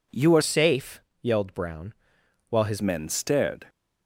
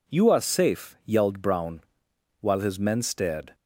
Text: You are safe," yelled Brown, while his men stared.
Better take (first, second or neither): second